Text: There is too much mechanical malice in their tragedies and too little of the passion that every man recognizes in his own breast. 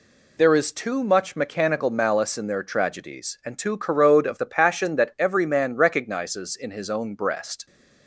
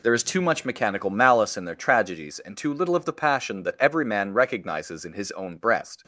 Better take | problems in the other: second | says "corrode" for "little"; at 3.7 s

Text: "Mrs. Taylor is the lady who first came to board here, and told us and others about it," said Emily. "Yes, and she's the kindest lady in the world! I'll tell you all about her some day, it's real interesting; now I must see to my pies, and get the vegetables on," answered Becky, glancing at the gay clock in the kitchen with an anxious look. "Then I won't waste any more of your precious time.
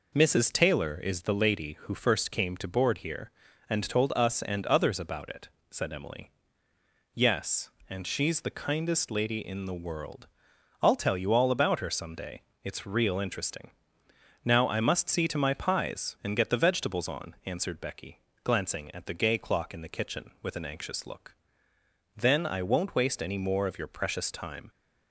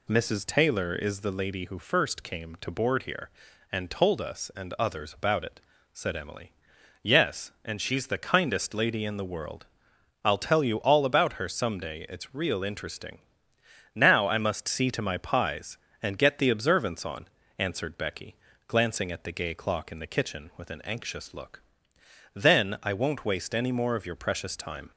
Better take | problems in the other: first | says "observance" for "vegetables"; at 16.5 s

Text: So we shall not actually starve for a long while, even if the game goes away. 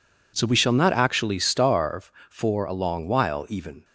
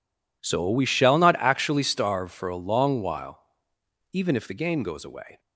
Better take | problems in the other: second | stops before "if the game goes away"; at 3.8 s

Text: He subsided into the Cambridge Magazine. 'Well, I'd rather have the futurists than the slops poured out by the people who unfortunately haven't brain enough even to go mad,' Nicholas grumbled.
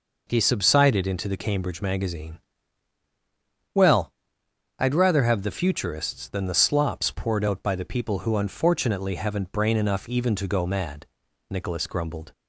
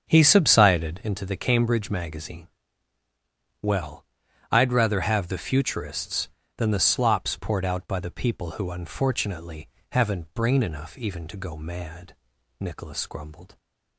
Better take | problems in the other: first | starts louder than the rest; strong; until 1.1 s; 7.5 dB // pauses between "unfortunately" and "haven't"; slight; at 9.6 s; 0.22 s long

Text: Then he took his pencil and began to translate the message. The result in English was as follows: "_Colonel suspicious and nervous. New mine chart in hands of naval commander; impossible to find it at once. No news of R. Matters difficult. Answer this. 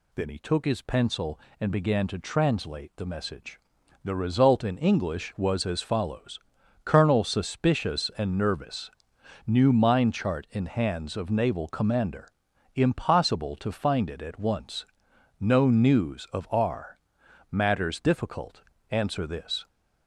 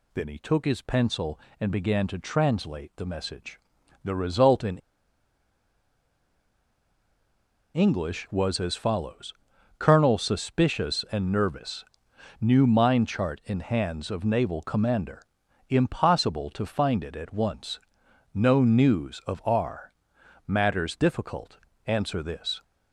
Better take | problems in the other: first | pauses between "in" and "English"; strong; at 4.7 s; 2.9 s long

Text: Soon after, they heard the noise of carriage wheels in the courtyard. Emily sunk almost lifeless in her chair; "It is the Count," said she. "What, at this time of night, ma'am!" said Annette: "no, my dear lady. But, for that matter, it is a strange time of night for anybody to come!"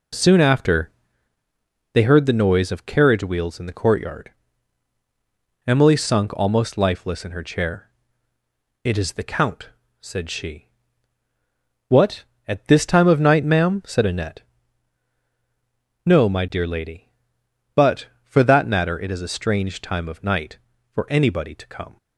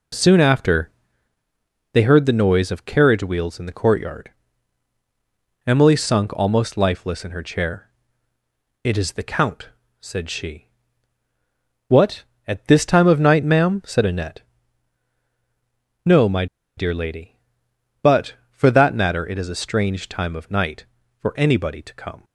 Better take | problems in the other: first | pauses between "my" and "dear"; slight; at 16.4 s; 0.31 s long

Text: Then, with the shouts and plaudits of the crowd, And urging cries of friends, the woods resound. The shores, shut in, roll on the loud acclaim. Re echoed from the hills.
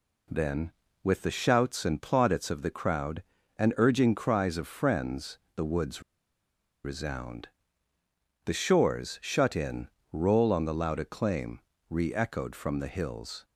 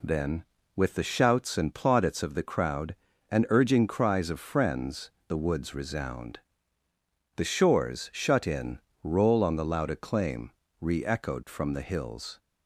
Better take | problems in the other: second | pauses between "woods" and "resound"; noticeable; at 6.0 s; 0.81 s long

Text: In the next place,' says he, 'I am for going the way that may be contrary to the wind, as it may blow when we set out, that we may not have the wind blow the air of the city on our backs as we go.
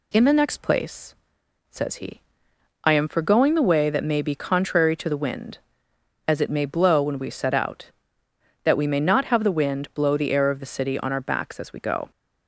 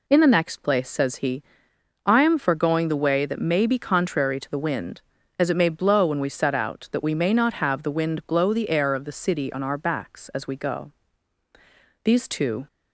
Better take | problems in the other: first | goes on to say "These two"; noticeable; from 12.0 s on; 0.64 s long

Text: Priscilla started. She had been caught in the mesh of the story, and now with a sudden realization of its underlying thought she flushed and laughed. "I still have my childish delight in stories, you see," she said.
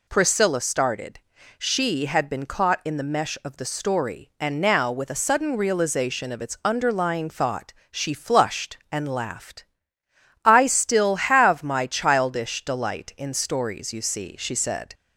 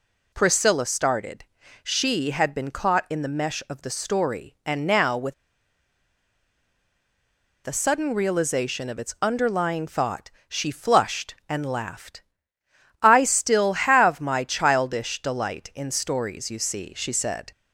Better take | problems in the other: first | pauses between "with" and "a"; strong; at 5.3 s; 2.3 s long // pauses between "thought" and "she"; slight; at 10.3 s; 0.16 s long; slight in the first

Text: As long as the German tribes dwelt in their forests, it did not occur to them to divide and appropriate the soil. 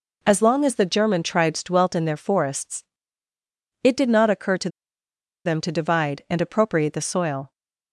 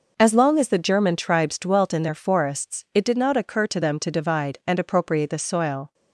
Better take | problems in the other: second | pauses between "to" and "them"; noticeable; at 4.6 s; 0.75 s long

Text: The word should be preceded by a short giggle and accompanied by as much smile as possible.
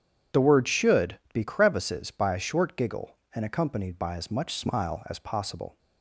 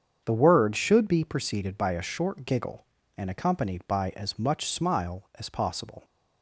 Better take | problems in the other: second | starts louder than the rest; strong; until 1.4 s; 9 dB; strong in the second // says "crevices" for "preceded"; at 1.4 s

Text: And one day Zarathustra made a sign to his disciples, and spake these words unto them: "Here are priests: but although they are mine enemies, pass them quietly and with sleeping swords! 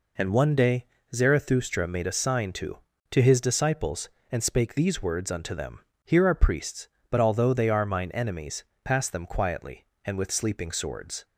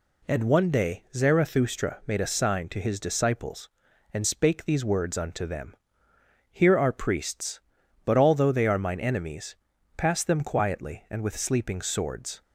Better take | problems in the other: second | pauses between "day" and "Zarathustra"; slight; at 0.8 s; 0.28 s long // says "to" twice; at 3.1 s

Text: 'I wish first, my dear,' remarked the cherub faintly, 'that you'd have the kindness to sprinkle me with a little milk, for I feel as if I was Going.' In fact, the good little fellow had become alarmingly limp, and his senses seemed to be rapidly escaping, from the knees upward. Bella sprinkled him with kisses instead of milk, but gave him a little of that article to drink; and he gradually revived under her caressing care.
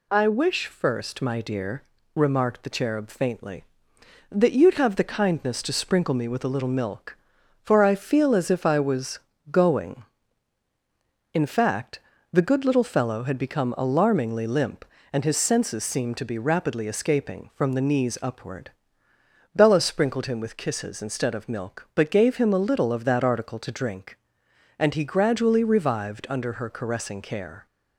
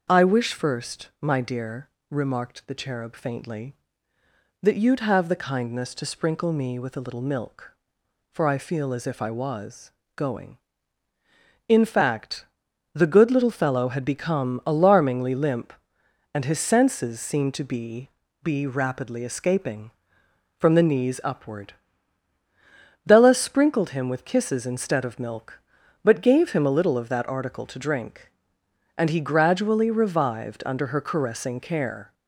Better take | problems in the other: first | starts louder than the rest; until 1.1 s; 6 dB // pauses between "was" and "Going"; slight; at 9.9 s; 0.24 s long; slight in the first // says "be" twice; at 18.4 s

